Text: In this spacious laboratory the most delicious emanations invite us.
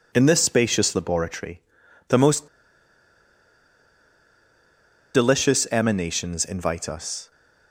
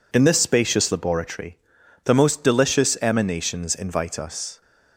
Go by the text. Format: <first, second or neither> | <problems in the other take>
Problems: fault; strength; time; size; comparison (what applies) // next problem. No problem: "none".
second | pauses between "laboratory" and "the"; noticeable; at 1.6 s; 0.46 s long; noticeable in the second // pauses between "most" and "delicious"; strong; at 2.4 s; 2.6 s long